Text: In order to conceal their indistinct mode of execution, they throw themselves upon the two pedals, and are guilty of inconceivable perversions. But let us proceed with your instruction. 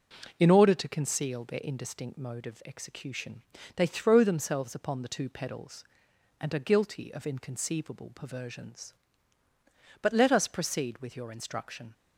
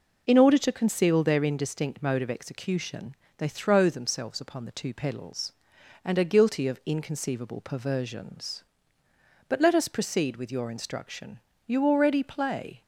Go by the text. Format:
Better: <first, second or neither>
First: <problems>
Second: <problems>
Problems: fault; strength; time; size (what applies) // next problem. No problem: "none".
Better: first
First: none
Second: goes on to say "You already play"; noticeable; from 11.6 s on; 1.1 s long